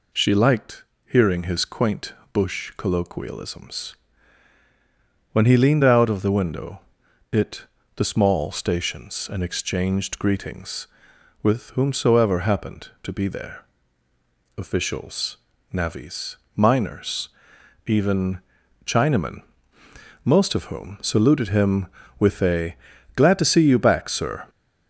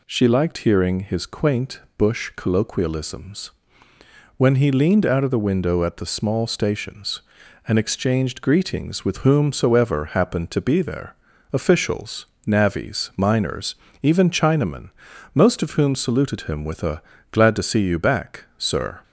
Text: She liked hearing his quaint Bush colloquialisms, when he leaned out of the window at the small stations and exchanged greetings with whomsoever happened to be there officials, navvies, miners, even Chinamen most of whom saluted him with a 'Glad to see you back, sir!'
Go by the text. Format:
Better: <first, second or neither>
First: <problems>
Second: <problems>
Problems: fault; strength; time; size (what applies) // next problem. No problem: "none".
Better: second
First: pauses between "liked" and "hearing"; slight; at 0.8 s; 0.22 s long // pauses between "quaint" and "Bush"; slight; at 2.1 s; 0.20 s long // says "it" for "at"; at 7.3 s // pauses between "there" and "officials"; noticeable; at 13.6 s; 0.94 s long // pauses between "even" and "Chinamen"; at 18.4 s; 0.44 s long // pauses between "Chinamen" and "most"; noticeable; at 19.4 s; 0.84 s long // pauses between "a" and "Glad"; at 22.7 s; 0.38 s long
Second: pauses between "quaint" and "Bush"; slight; at 1.7 s; 0.18 s long // pauses between "there" and "officials"; at 11.1 s; 0.38 s long // pauses between "Chinamen" and "most"; noticeable; at 14.8 s; 0.46 s long // pauses between "a" and "Glad"; slight; at 17.0 s; 0.30 s long